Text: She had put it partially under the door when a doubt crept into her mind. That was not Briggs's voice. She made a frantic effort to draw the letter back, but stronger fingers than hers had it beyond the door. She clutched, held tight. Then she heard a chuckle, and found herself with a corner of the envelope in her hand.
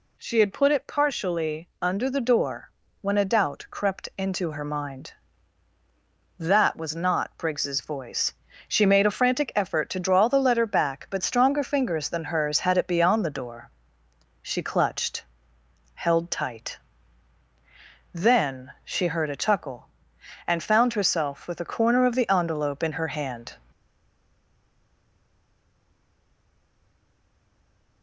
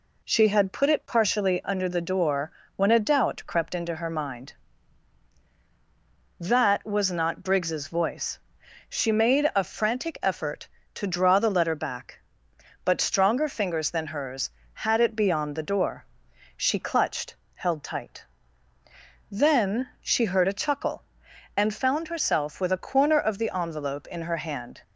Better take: second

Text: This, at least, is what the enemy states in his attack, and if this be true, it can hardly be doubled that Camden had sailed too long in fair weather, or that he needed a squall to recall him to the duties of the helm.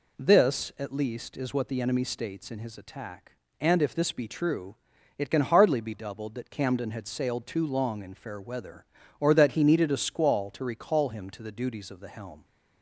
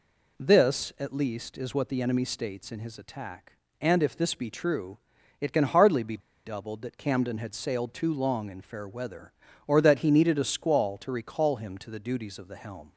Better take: first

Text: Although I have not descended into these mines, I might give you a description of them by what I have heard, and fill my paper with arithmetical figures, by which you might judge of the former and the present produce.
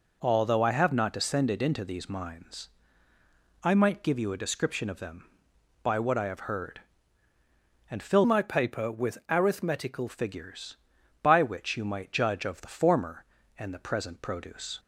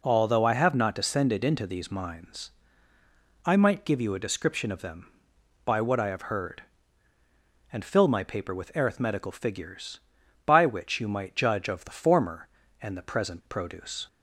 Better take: second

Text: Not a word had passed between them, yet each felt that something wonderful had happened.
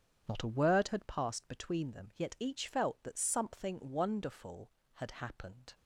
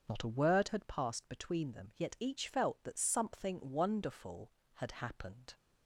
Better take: second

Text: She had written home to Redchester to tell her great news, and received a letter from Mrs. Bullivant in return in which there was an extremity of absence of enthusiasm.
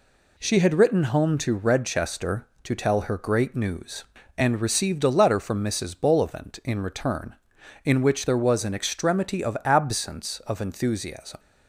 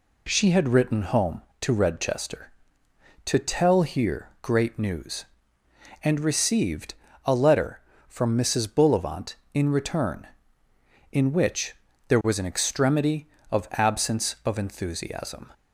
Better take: first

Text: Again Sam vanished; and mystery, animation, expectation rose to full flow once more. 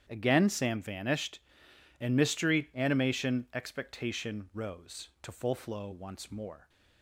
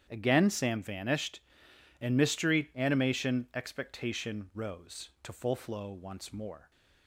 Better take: neither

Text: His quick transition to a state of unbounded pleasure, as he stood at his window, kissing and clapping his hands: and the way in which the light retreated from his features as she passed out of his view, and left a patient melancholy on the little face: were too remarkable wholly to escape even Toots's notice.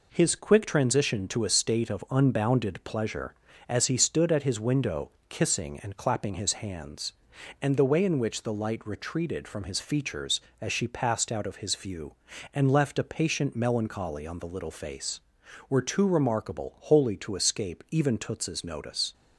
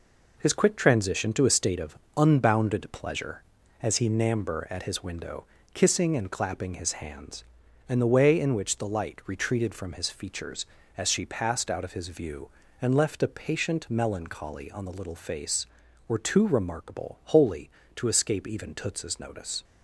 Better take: first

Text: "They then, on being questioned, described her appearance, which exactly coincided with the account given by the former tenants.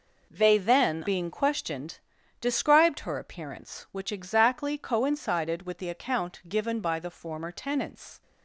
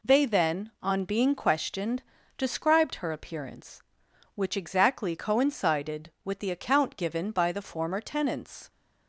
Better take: second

